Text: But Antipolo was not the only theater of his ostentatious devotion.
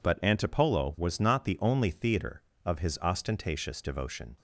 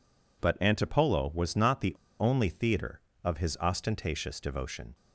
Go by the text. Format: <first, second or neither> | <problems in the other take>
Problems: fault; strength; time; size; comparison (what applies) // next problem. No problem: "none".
first | pauses between "the" and "only"; slight; at 1.9 s; 0.25 s long